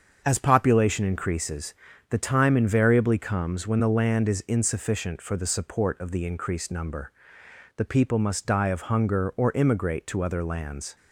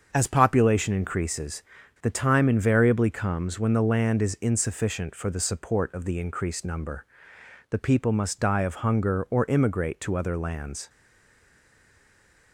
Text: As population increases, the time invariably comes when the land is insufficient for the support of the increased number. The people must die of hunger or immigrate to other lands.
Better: first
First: starts louder than the rest; until 1.2 s; 7 dB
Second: starts louder than the rest; until 1.1 s; 7 dB // stays silent after the last word; noticeable; from 10.8 s on; 1.7 s long

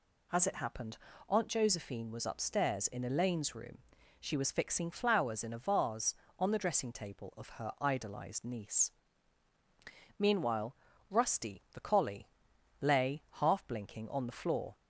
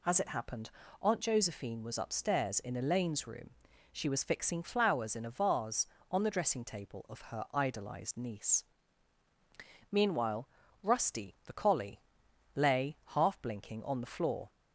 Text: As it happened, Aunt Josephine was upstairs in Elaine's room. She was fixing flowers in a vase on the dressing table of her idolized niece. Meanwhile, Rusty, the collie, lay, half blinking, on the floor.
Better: neither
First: none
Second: none

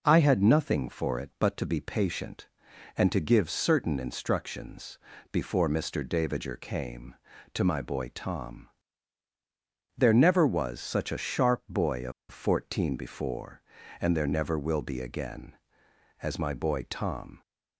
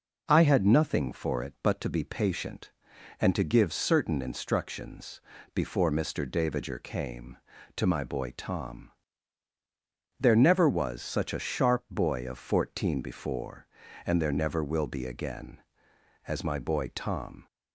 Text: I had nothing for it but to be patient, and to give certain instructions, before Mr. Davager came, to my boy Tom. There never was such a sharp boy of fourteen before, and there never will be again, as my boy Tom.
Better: second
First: pauses between "of" and "fourteen"; slight; at 12.1 s; 0.18 s long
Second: none

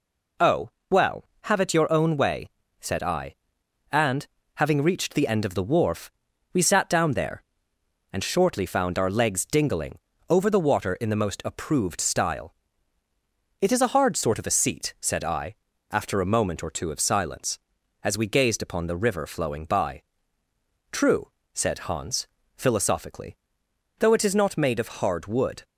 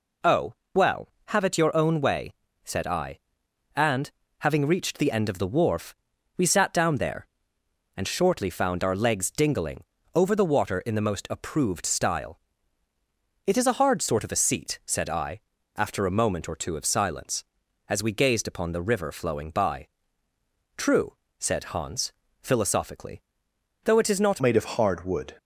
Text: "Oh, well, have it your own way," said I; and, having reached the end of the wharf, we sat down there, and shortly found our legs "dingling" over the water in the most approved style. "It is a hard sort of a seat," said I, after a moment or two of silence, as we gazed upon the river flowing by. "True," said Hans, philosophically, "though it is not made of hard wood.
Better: first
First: pauses between "dingling" and "over"; slight; at 9.9 s; 0.32 s long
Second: pauses between "dingling" and "over"; slight; at 9.8 s; 0.32 s long // changes voice at "made"; from 24.4 s on; 0.9 s long

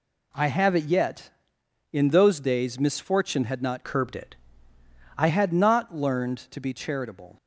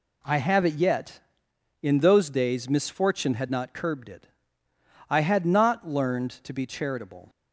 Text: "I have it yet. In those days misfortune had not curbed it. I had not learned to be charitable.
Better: second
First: changes voice from "curbed" to "I"; from 3.8 to 5.2 s; 1.4 s long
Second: none

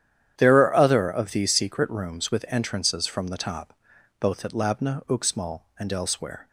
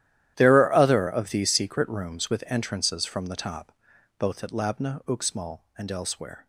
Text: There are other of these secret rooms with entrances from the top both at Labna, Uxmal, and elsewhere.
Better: first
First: starts louder than the rest; strong; until 1.4 s; 10 dB // pauses between "top" and "both"; noticeable; at 3.7 s; 0.46 s long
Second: gets quieter; strong; throughout; 17.5 dB // starts louder than the rest; strong; until 1.3 s; 12 dB // pauses between "top" and "both"; noticeable; at 3.7 s; 0.46 s long

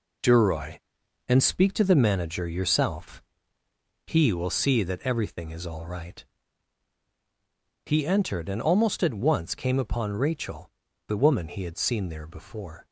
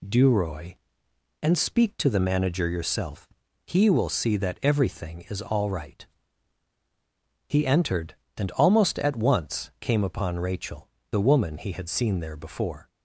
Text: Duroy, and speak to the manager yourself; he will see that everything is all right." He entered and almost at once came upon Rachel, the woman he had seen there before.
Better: second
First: gets quieter; strong; throughout; 7 dB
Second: none

